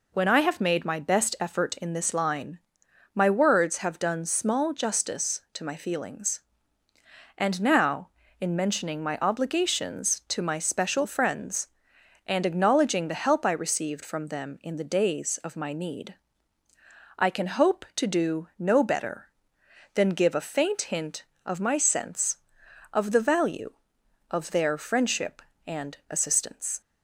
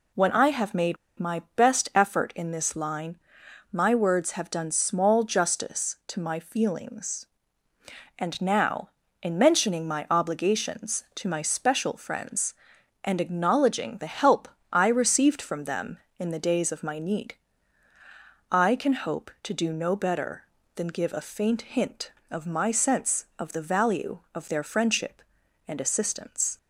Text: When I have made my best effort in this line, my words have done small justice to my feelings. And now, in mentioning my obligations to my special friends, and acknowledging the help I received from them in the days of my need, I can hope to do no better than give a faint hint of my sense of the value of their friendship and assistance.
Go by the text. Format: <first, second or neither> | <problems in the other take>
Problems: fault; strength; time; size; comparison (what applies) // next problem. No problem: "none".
first | pauses between "made" and "my"; slight; at 0.9 s; 0.22 s long // pauses between "help" and "I"; slight; at 14.4 s; 0.24 s long